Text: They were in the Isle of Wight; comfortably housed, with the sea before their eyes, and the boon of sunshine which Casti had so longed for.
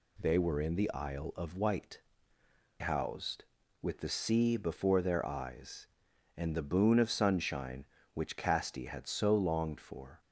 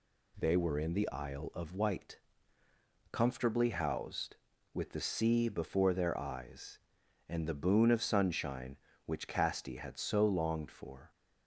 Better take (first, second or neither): second